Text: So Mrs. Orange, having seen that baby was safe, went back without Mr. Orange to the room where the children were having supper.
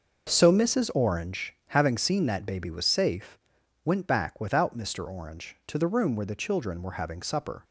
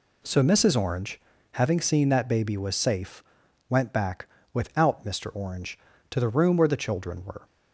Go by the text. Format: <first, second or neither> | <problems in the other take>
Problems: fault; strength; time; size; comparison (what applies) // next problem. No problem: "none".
first | pauses between "back" and "without"; slight; at 4.2 s; 0.26 s long // stops before "having supper"; at 7.4 s